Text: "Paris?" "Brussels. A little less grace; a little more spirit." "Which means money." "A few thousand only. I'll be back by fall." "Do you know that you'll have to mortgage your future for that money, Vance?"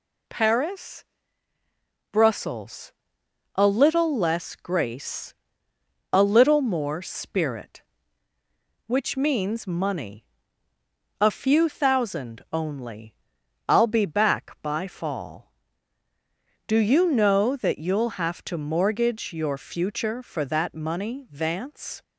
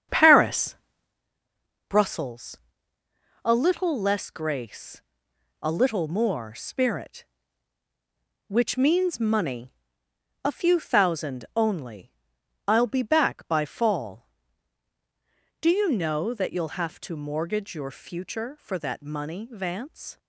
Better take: first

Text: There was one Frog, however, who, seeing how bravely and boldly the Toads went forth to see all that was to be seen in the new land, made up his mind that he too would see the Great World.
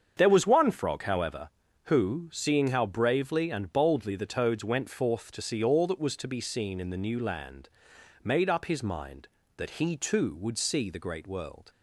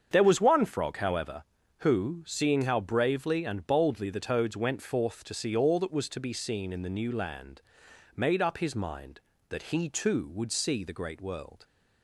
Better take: neither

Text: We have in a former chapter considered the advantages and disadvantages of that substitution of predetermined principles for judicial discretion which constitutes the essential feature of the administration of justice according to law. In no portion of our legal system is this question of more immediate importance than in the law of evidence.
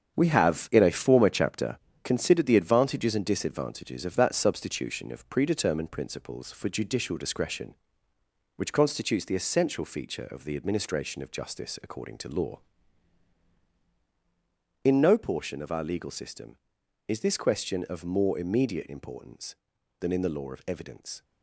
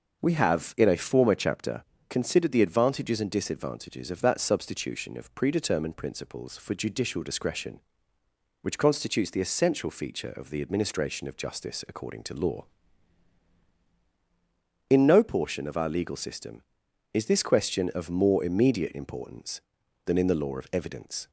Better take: second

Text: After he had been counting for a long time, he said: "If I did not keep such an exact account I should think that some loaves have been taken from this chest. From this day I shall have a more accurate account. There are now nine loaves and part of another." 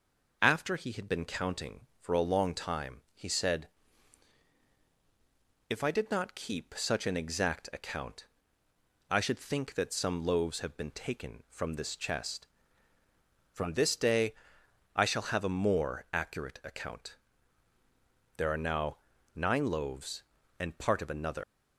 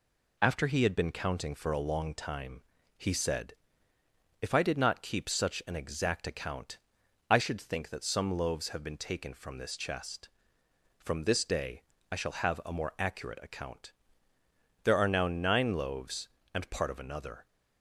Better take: second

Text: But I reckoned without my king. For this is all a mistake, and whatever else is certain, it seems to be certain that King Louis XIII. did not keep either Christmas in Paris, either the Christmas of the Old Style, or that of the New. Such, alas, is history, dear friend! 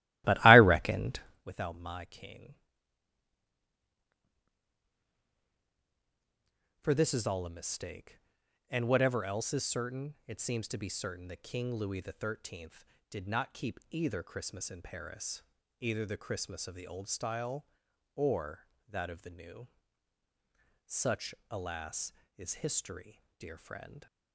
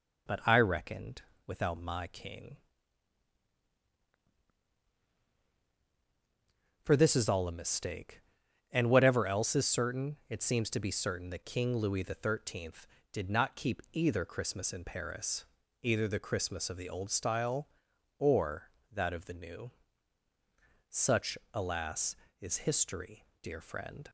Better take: second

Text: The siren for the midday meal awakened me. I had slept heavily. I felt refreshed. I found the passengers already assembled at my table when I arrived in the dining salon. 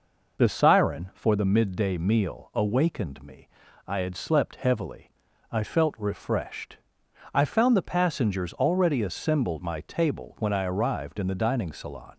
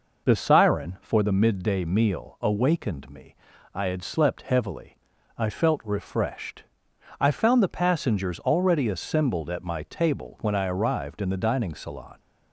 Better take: second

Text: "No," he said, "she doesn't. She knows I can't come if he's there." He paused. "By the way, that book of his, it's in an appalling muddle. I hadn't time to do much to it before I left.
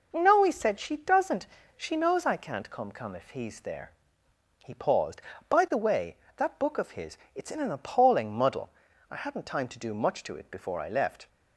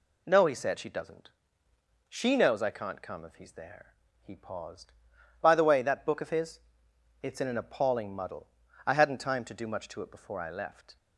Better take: second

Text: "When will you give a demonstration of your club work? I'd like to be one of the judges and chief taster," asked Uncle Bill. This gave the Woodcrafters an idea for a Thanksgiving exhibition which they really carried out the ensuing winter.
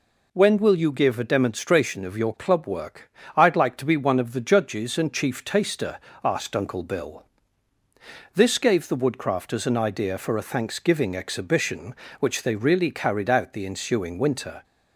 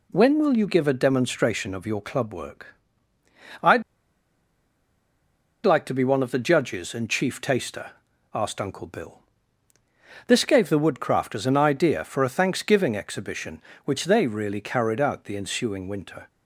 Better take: first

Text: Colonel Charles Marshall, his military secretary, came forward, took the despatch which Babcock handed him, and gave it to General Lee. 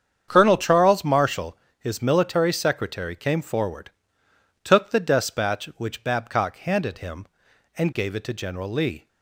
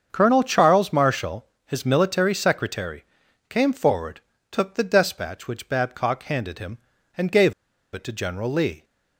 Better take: first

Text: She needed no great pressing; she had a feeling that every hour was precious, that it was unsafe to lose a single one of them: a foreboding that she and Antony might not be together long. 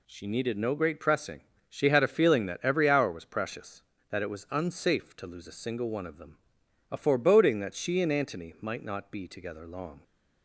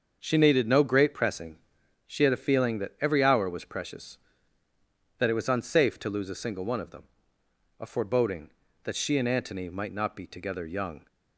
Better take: first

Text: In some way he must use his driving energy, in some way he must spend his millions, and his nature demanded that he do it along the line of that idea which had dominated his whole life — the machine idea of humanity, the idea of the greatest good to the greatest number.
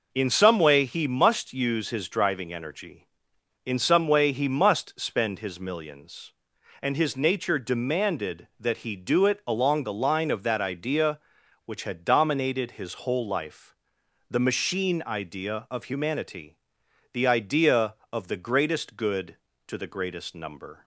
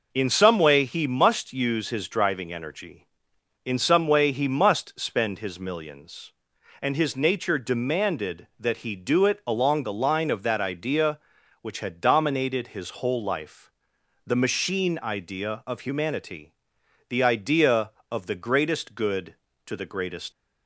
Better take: first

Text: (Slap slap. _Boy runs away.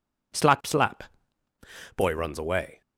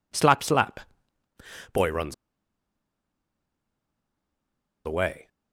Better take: first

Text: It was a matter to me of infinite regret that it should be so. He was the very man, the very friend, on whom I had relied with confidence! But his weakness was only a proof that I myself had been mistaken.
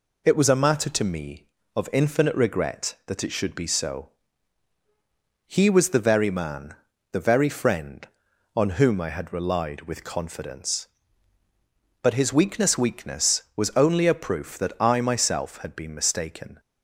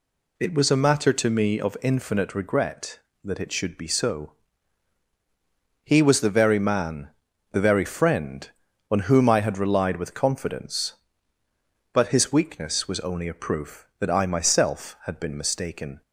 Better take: second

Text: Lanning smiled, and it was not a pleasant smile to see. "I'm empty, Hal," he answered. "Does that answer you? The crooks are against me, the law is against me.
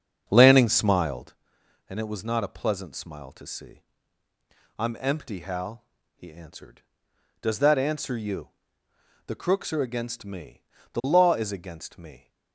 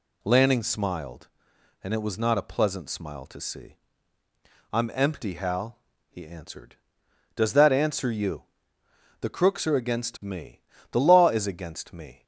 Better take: second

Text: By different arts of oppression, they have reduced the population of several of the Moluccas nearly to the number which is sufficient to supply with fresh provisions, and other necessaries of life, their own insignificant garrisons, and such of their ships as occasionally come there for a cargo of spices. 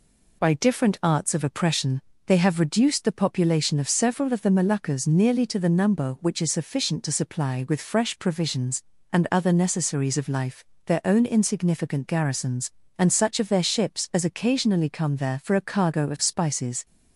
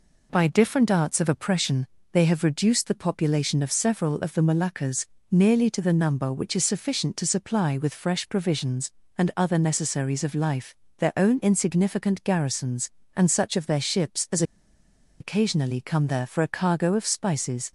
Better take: first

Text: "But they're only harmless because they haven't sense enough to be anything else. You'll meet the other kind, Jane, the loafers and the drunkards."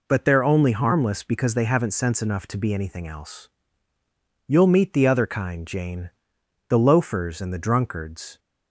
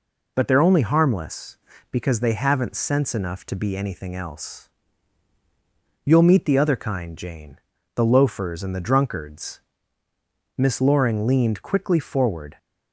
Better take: first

